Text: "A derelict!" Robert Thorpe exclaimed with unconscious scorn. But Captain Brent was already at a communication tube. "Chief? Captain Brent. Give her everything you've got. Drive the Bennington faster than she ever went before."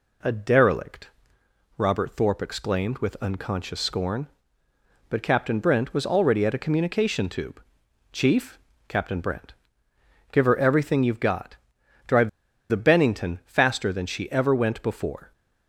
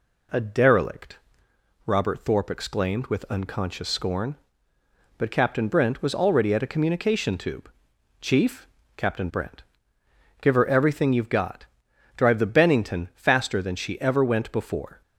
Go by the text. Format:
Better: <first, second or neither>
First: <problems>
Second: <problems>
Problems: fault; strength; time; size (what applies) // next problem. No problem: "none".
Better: second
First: pauses between "Drive" and "the"; at 12.2 s; 0.40 s long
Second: none